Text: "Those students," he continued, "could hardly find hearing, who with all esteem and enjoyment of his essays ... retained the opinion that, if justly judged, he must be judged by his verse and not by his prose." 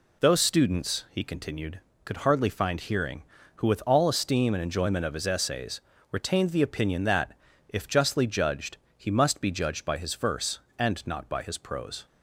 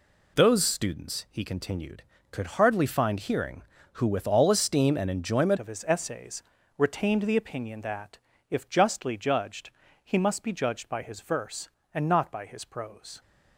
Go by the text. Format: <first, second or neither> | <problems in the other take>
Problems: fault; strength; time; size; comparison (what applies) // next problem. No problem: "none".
first | changes voice at "of"; from 5.5 s on; 7.7 s long